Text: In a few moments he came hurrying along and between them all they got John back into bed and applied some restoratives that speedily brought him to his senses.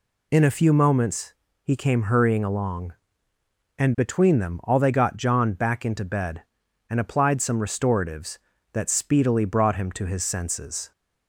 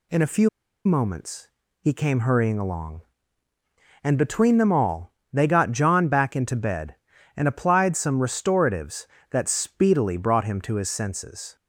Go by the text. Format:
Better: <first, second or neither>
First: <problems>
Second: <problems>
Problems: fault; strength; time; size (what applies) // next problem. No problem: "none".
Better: first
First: pauses between "moments" and "he"; slight; at 1.3 s; 0.30 s long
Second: pauses between "few" and "moments"; at 0.4 s; 0.36 s long // pauses between "moments" and "he"; slight; at 1.4 s; 0.34 s long // pauses between "all" and "they"; slight; at 5.1 s; 0.22 s long